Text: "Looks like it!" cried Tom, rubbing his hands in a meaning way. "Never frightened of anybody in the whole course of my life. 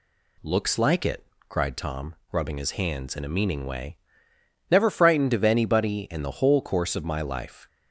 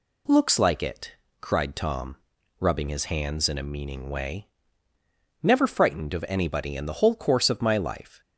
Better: neither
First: none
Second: none

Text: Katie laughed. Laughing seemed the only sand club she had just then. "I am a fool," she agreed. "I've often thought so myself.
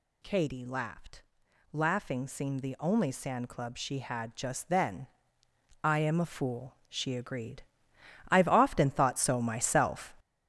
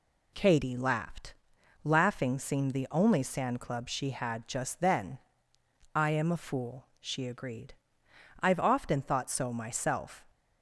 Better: second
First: gets louder; strong; throughout; 8 dB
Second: none

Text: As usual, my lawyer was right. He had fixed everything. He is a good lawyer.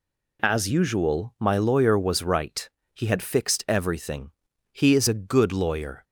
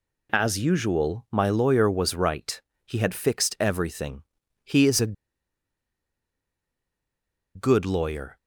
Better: first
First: none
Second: pauses between "a" and "good"; strong; at 5.1 s; 2.4 s long

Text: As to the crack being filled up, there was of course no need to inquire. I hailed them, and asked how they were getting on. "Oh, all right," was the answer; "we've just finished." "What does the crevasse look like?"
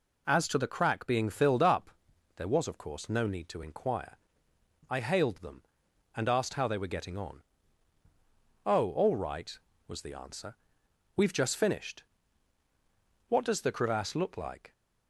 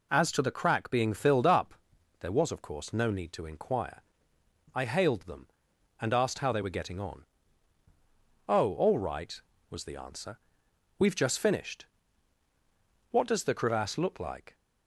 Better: neither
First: none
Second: none

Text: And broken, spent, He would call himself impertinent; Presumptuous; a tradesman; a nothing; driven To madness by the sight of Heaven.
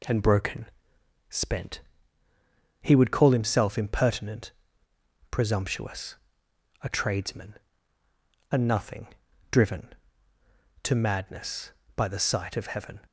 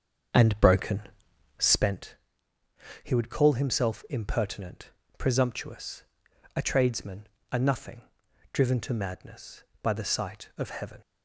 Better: first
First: none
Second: starts louder than the rest; strong; until 1.9 s; 7 dB

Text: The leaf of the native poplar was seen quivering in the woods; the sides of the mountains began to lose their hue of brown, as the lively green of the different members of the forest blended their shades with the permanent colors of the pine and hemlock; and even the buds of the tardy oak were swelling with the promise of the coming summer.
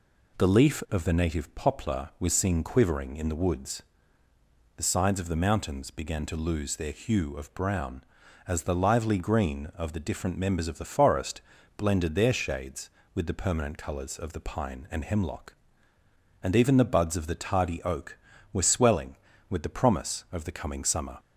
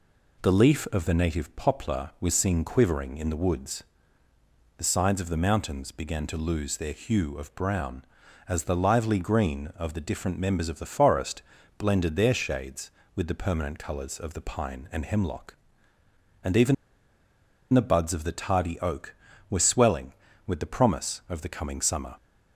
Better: first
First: pauses between "forest" and "blended"; slight; at 11.4 s; 0.36 s long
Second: pauses between "forest" and "blended"; slight; at 11.4 s; 0.36 s long // pauses between "even" and "the"; at 16.7 s; 0.98 s long

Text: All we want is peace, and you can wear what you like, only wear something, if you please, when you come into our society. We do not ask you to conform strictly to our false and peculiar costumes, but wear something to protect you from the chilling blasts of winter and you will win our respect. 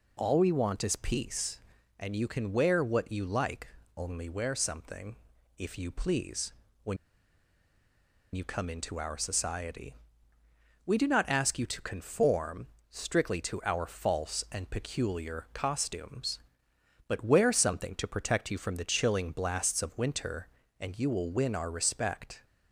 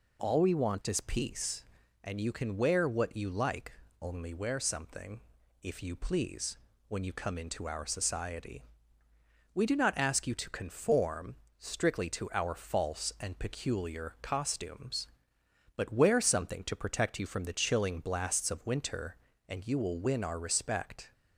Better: second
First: pauses between "when" and "you"; strong; at 6.9 s; 1.3 s long // pauses between "conform" and "strictly"; slight; at 12.6 s; 0.24 s long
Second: pauses between "conform" and "strictly"; slight; at 11.3 s; 0.24 s long

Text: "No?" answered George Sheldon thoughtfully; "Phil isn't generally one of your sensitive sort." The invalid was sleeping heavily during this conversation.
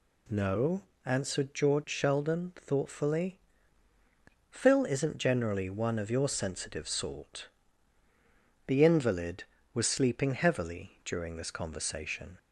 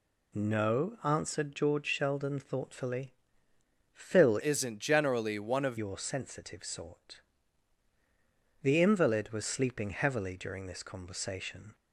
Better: first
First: none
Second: changes voice from "isn't" to "of"; from 4.4 to 5.7 s; 1.3 s long

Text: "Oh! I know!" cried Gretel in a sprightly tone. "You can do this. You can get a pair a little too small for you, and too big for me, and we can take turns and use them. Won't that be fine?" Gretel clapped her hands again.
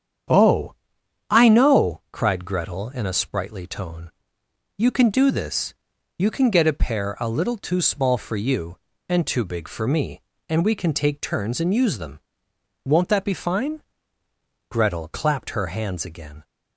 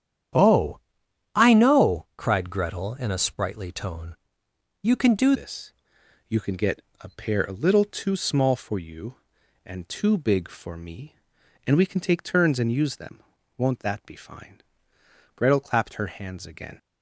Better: first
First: starts louder than the rest; strong; until 1.8 s; 8.5 dB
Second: starts louder than the rest; strong; until 1.9 s; 9.5 dB // changes voice at "this"; from 5.3 s on; 11.4 s long // pauses between "get" and "a"; slight; at 6.7 s; 0.20 s long

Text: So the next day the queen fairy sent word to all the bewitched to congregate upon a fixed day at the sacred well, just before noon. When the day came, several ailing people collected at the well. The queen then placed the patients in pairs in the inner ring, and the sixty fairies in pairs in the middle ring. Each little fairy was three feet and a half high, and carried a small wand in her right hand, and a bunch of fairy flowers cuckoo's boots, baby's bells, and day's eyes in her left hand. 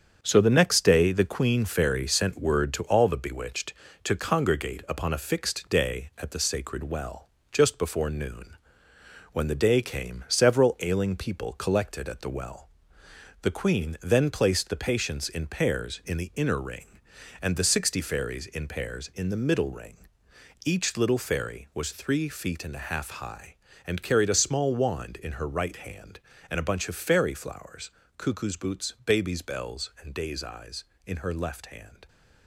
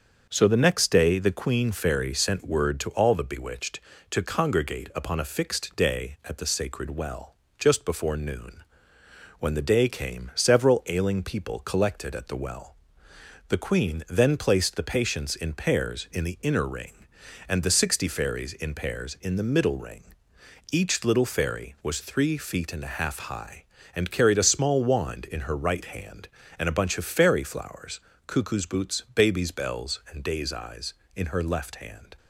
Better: second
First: gets quieter; noticeable; throughout; 6 dB // starts louder than the rest; strong; until 1.2 s; 7.5 dB // pauses between "flowers" and "cuckoo's"; slight; at 27.9 s; 0.24 s long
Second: starts louder than the rest; until 1.3 s; 7 dB // pauses between "flowers" and "cuckoo's"; slight; at 28.0 s; 0.24 s long

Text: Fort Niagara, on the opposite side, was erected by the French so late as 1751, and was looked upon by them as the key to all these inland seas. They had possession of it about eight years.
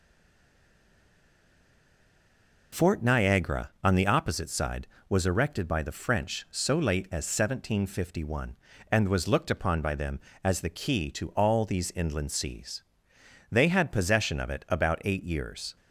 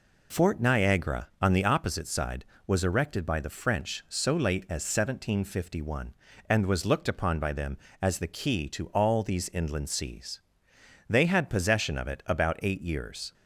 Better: second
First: stays silent before the first word; strong; until 2.7 s; 2.7 s long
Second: none

